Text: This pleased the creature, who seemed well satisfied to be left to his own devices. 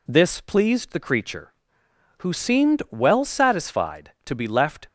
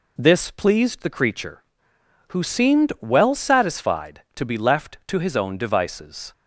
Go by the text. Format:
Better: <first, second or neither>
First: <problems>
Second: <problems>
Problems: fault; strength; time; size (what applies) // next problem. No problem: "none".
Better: second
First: stops before "to his own devices"; at 4.8 s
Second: none